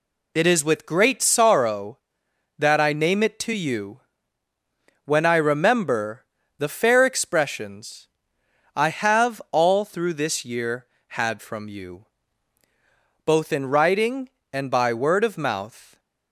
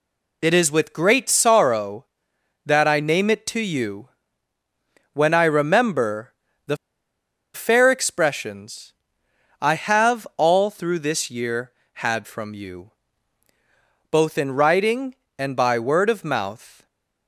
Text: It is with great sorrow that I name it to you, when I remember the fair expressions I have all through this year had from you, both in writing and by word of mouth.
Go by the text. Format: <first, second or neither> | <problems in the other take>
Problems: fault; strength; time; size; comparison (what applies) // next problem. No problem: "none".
first | pauses between "remember" and "the"; slight; at 6.3 s; 0.34 s long; slight in the first // pauses between "the" and "fair"; noticeable; at 6.7 s; 0.77 s long // pauses between "expressions" and "I"; noticeable; at 8.9 s; 0.70 s long; noticeable in the first